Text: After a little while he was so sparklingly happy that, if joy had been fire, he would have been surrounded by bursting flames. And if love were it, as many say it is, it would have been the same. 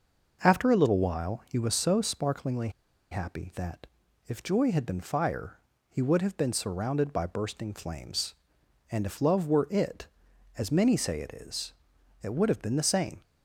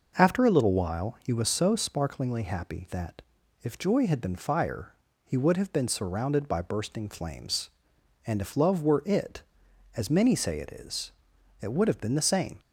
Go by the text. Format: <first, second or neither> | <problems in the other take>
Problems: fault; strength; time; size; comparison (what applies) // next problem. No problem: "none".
second | pauses between "sparklingly" and "happy"; at 2.6 s; 0.41 s long